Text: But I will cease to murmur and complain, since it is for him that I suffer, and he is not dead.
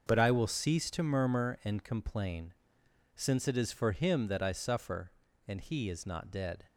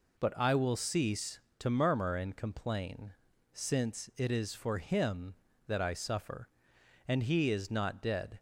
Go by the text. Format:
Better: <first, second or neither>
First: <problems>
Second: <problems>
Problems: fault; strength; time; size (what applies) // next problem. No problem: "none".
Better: neither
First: none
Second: none